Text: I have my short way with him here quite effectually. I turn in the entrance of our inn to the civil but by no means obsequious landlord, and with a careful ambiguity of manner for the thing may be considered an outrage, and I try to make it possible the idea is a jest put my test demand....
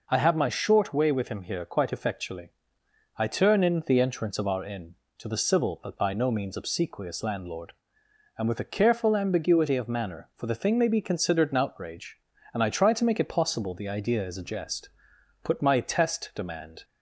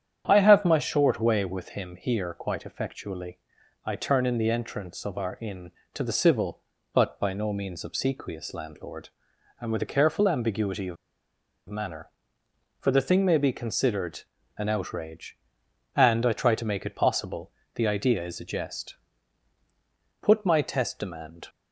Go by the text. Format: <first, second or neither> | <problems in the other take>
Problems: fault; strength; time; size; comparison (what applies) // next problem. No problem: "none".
first | starts louder than the rest; strong; until 1.2 s; 9 dB // pauses between "of" and "manner"; noticeable; at 10.9 s; 0.72 s long // pauses between "considered" and "an"; slight; at 14.2 s; 0.36 s long // pauses between "possible" and "the"; slight; at 17.5 s; 0.24 s long // pauses between "jest" and "put"; strong; at 18.9 s; 1.2 s long; noticeable in the first